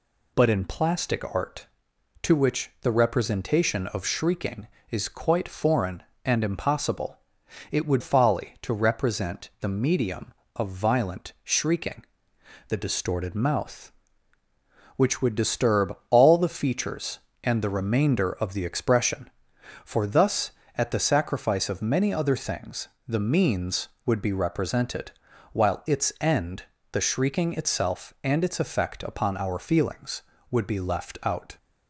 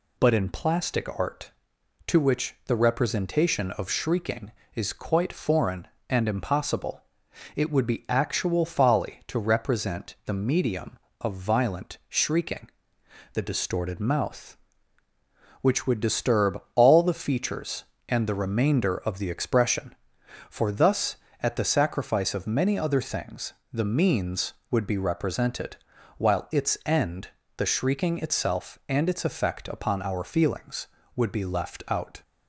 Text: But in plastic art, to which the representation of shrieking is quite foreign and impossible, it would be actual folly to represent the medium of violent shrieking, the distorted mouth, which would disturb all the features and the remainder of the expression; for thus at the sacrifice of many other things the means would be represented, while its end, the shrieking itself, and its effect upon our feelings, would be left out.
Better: second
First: skips "be actual"; at 8.0 s // pauses between "things" and "the"; slight; at 22.8 s; 0.20 s long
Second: pauses between "things" and "the"; slight; at 23.5 s; 0.20 s long

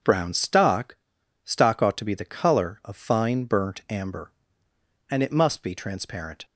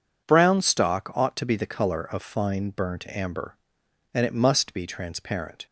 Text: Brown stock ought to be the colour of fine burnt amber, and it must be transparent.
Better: second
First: starts louder than the rest; until 1.5 s; 6 dB // says "stock" twice; at 1.4 s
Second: none

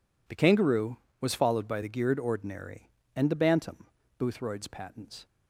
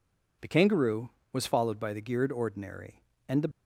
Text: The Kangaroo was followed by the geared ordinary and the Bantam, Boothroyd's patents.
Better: first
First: none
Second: stops before "Bantam Boothroyd's patents"; at 3.5 s

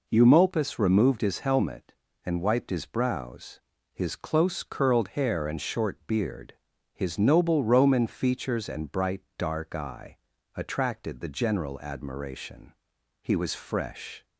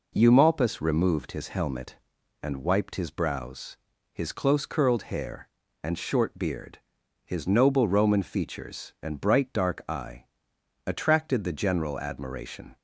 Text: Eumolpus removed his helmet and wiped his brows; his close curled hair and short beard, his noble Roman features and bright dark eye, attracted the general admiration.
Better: second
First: pauses between "bright" and "dark"; slight; at 9.2 s; 0.16 s long // goes on to say "He was fresh"; noticeable; from 13.2 s on; 1.0 s long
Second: none

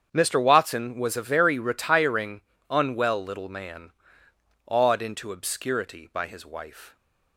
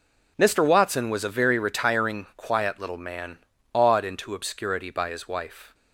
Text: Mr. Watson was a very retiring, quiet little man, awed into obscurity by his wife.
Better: second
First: starts louder than the rest; strong; until 1.1 s; 8 dB // says "unwell" for "quiet"; at 2.6 s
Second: none

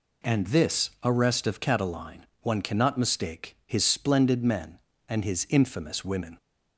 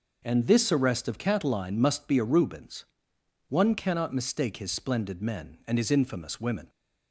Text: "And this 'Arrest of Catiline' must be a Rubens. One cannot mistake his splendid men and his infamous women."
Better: second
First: skips "must be a Rubens"; at 2.3 s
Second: none

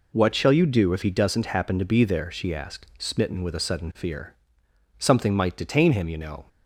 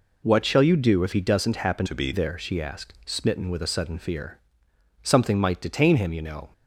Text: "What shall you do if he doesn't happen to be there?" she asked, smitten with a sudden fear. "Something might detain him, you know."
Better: first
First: none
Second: changes voice from "to" to "be"; from 1.8 to 2.1 s; 0.3 s long

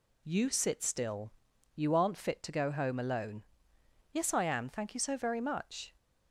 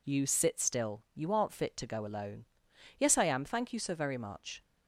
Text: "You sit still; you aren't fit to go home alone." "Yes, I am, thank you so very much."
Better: first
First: none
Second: skips "home"; at 2.0 s

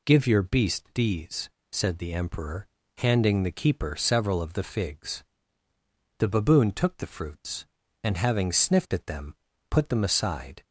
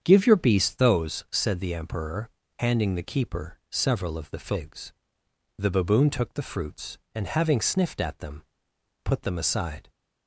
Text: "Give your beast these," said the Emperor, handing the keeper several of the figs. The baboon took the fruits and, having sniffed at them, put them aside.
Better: first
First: none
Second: starts louder than the rest; strong; until 1.0 s; 8 dB // says "those" for "these"; at 0.7 s

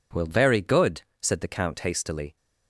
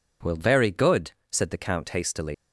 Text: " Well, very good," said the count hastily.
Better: first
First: none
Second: leaves "hastily" unfinished; at 2.3 s; 110 ms

